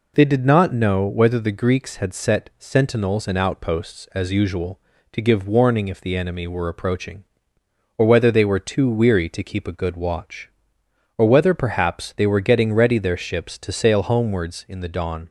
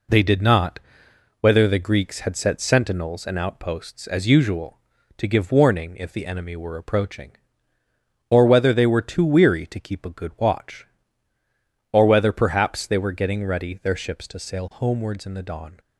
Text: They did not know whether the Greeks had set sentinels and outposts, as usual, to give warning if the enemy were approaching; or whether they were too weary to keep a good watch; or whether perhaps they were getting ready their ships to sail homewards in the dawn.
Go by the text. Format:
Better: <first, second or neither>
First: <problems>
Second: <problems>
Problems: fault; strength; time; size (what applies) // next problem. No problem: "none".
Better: first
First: none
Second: skips "know"; at 1.0 s